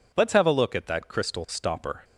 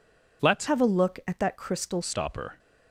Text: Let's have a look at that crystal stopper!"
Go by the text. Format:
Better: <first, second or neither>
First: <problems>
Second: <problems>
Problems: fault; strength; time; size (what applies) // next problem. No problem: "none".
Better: first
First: none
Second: changes voice from "have" to "crystal"; from 0.6 to 2.0 s; 1.4 s long